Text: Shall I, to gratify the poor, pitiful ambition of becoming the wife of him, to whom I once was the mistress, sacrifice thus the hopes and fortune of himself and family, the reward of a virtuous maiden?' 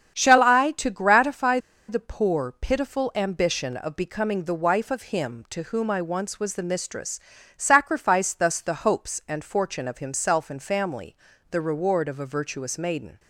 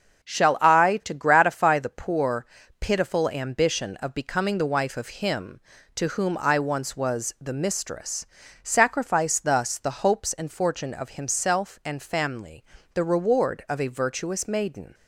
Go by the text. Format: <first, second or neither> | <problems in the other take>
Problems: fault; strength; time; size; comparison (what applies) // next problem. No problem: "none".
second | starts louder than the rest; strong; until 1.2 s; 8.5 dB; strong in the second // pauses between "gratify" and "the"; slight; at 1.5 s; 0.30 s long